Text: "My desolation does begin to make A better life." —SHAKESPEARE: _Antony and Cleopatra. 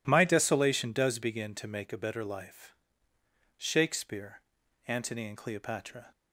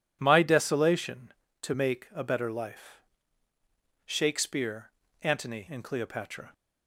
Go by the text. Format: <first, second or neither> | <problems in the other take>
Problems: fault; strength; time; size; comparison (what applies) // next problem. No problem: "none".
first | skips "does begin"; at 1.4 s